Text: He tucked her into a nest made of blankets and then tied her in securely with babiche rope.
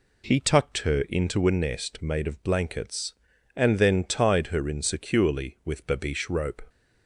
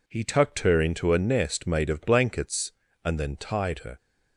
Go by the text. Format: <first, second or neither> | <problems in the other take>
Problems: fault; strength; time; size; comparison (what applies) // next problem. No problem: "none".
first | stops before "in securely with babiche rope"; at 3.9 s